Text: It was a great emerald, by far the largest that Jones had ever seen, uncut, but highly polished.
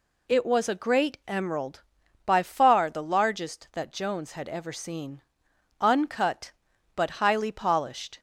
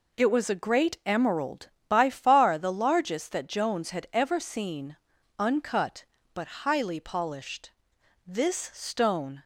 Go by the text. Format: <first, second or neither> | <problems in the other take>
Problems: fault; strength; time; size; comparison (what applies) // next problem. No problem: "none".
first | goes on to say "This stone"; noticeable; from 8.2 s on; 1.1 s long